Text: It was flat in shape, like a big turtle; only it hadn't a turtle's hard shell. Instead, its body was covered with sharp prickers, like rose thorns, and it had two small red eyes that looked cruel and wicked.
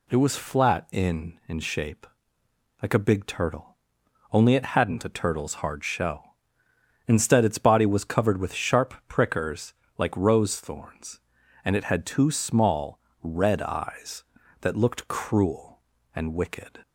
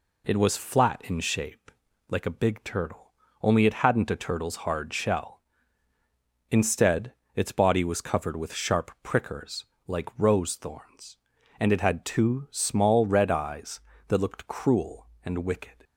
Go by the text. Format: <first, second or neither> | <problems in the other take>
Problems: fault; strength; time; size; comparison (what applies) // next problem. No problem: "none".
second | says "in" twice; at 1.4 s // pauses between "small" and "red"; slight; at 12.9 s; 0.22 s long